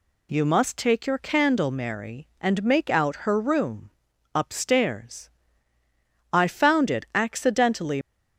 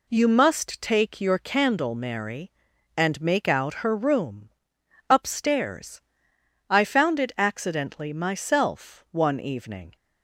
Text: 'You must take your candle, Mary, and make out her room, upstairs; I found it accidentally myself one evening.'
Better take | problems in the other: second | stops before "myself one evening"; at 8.0 s

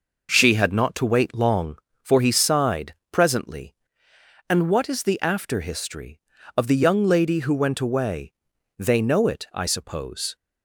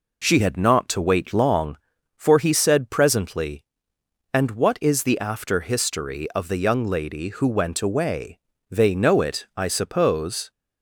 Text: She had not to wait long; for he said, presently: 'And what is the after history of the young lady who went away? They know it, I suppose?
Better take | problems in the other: second | says "sighed" for "said"; at 2.2 s

